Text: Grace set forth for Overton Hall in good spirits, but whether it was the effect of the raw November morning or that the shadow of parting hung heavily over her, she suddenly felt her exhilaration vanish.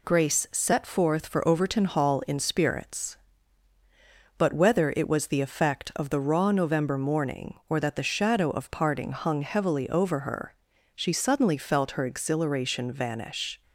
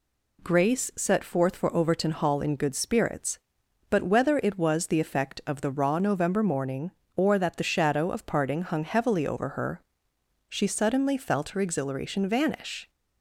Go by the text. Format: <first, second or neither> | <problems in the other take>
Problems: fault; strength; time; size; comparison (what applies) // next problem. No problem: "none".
second | skips "good"; at 2.3 s